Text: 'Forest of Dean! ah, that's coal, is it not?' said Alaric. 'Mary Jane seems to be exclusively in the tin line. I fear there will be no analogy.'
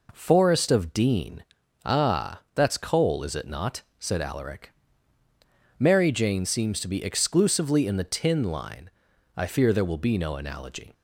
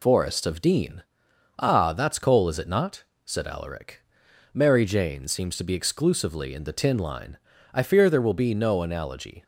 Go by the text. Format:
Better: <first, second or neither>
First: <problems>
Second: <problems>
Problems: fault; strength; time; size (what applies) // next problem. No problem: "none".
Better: neither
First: none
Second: none